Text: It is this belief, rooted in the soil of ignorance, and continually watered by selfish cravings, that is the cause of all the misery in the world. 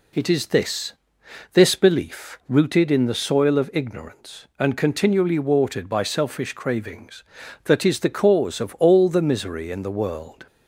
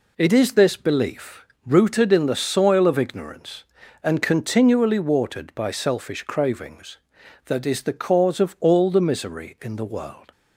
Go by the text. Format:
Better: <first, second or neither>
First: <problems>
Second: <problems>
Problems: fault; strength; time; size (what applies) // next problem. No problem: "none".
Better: second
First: says "this" twice; at 1.5 s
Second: none